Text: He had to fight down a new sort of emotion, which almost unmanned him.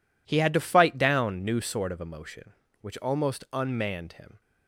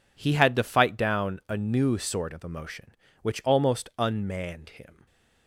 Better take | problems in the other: second | skips "a"; at 1.4 s

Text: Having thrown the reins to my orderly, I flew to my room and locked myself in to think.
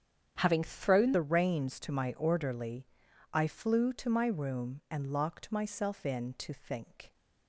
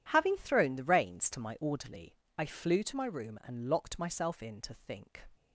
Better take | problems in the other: second | starts louder than the rest; strong; until 1.4 s; 9 dB // changes voice at "the"; from 1.1 s on; 6.0 s long

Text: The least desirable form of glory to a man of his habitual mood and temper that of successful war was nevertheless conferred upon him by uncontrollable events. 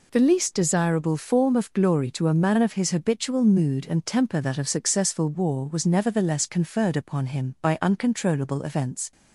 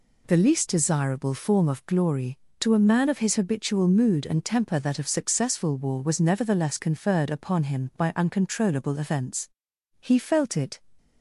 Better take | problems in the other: first | goes on to say "He felt it"; noticeable; from 9.9 s on; 0.80 s long

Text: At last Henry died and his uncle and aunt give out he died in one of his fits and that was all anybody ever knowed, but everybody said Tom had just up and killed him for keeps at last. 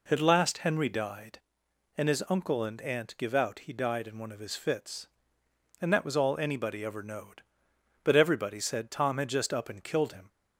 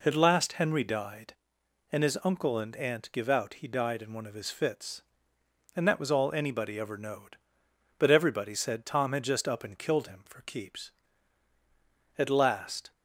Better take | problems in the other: second | stops before "for keeps at last"; at 10.2 s

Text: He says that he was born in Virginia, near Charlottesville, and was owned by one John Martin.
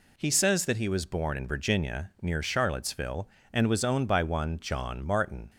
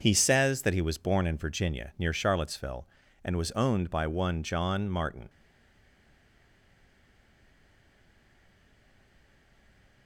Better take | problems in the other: first | stays silent after the last word; strong; from 5.2 s on; 4.8 s long

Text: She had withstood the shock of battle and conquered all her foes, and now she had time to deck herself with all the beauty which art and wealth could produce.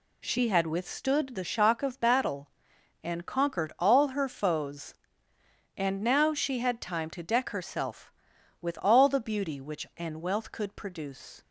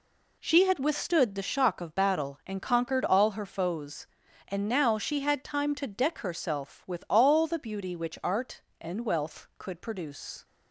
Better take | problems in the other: second | skips "art"; at 9.9 s

